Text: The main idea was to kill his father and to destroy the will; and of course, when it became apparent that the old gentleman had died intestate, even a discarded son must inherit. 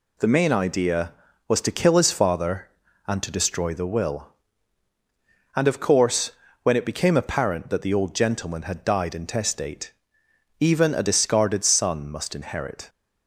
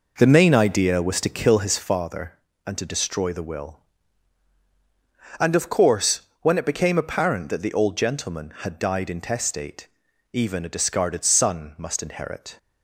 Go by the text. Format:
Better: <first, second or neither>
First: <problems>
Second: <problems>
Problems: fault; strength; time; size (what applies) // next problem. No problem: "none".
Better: first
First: none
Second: starts louder than the rest; noticeable; until 2.0 s; 5 dB